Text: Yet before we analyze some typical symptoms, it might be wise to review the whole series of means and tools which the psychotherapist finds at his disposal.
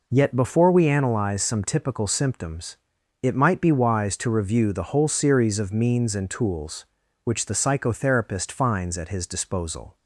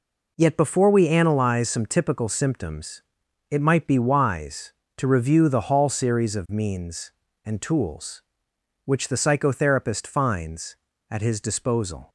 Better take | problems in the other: first | says "hall" for "whole"; at 5.6 s

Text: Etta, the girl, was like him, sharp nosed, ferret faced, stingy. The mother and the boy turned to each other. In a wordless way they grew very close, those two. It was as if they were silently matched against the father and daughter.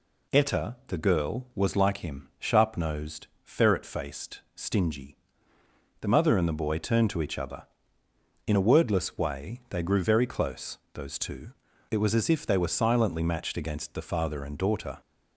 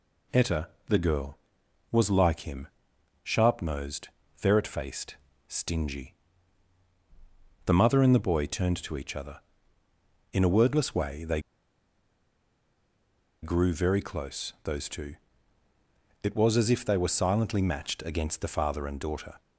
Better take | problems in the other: first | pauses between "they" and "grew"; strong; at 11.4 s; 2.0 s long

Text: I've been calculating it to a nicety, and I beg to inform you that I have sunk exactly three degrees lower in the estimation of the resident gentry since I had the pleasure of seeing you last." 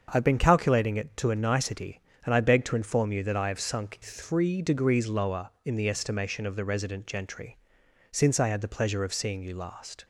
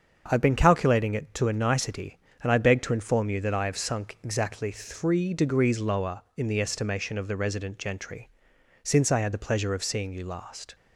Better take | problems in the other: second | starts louder than the rest; until 1.1 s; 7 dB; also in the second // skips "exactly"; at 4.0 s // pauses between "gentry" and "since"; noticeable; at 7.5 s; 0.54 s long; noticeable in the second

